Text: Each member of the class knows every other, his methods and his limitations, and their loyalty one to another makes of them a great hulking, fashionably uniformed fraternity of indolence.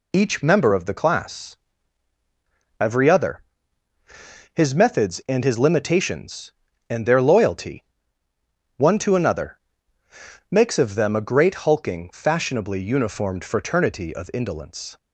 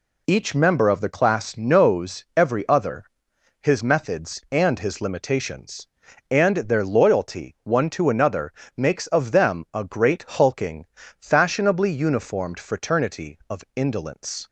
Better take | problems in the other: second | skips "knows"; at 2.1 s // pauses between "loyalty" and "one"; noticeable; at 7.8 s; 0.94 s long // pauses between "another" and "makes"; noticeable; at 9.5 s; 0.90 s long; slight in the second

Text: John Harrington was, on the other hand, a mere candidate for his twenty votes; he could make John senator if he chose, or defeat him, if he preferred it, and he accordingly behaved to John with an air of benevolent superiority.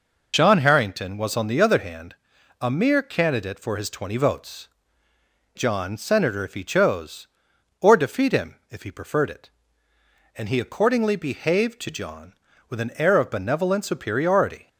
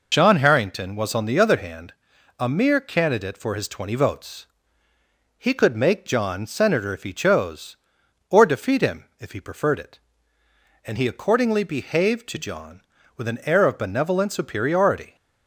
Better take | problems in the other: second | skips "he could make"; at 5.1 s

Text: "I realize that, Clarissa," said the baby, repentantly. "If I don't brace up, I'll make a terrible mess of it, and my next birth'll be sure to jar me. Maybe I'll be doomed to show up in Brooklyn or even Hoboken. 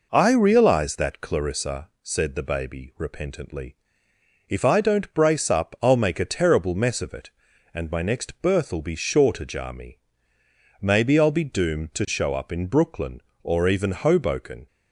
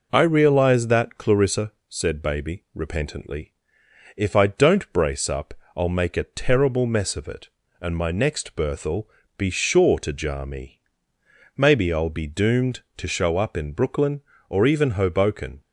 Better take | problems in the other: first | skips "the"; at 2.2 s // pauses between "birth'll" and "be"; slight; at 9.0 s; 0.30 s long

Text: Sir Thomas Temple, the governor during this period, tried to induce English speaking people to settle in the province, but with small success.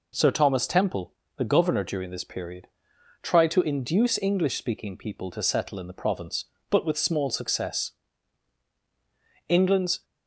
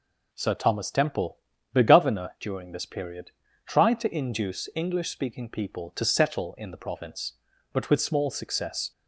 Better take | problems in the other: second | goes on to say "England's"; from 9.4 s on; 0.56 s long

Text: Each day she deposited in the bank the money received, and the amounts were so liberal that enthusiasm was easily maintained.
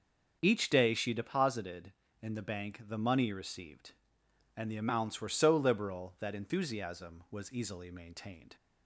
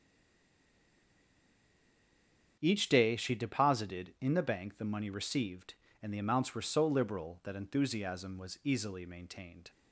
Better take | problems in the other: first | stays silent before the first word; strong; until 2.5 s; 2.5 s long // starts louder than the rest; until 3.6 s; 6.5 dB; also in the first

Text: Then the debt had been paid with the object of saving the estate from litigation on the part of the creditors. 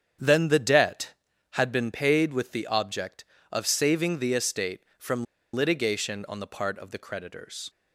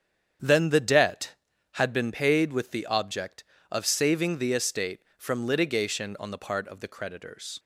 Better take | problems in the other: second | starts louder than the rest; strong; until 1.5 s; 8 dB; strong in the second // pauses between "from" and "litigation"; slight; at 5.2 s; 0.28 s long

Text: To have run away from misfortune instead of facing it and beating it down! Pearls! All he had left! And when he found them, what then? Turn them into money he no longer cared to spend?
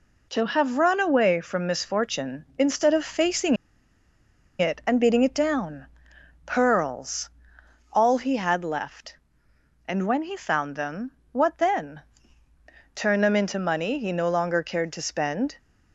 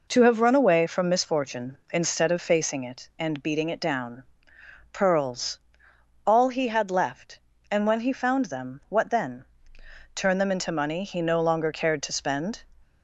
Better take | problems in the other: second | pauses between "facing" and "it"; at 3.5 s; 1.0 s long

